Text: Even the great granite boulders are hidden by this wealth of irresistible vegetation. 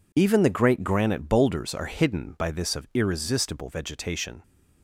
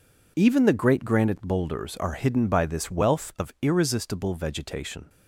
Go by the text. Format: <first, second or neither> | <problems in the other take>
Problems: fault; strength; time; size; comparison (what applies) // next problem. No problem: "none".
second | skips "wealth"; at 2.7 s